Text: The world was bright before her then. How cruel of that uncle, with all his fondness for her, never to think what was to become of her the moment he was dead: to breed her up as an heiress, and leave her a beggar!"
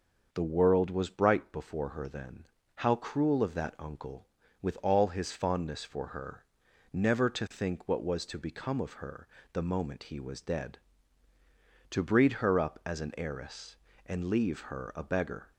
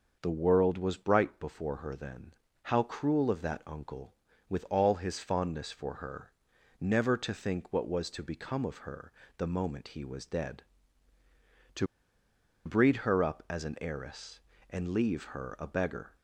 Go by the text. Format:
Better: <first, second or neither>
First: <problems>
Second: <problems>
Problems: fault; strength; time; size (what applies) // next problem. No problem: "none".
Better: first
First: starts louder than the rest; until 1.3 s; 6.5 dB // pauses between "her" and "the"; slight; at 9.2 s; 0.24 s long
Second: starts louder than the rest; until 1.2 s; 6.5 dB // pauses between "her" and "the"; slight; at 9.1 s; 0.24 s long // pauses between "to" and "breed"; noticeable; at 11.8 s; 0.79 s long